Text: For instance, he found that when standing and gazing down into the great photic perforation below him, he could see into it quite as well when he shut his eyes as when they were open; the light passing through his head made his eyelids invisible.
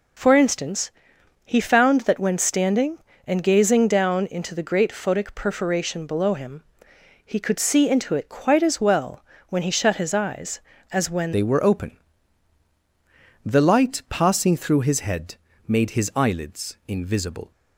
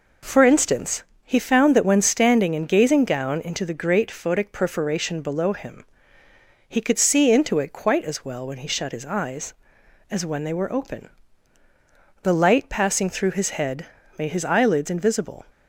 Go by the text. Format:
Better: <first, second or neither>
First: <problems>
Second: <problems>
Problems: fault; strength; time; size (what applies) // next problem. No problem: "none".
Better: second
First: pauses between "well" and "when"; slight; at 9.2 s; 0.28 s long // changes voice at "they"; from 11.3 s on; 6.2 s long // pauses between "head" and "made"; slight; at 15.3 s; 0.32 s long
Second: pauses between "head" and "made"; slight; at 13.8 s; 0.32 s long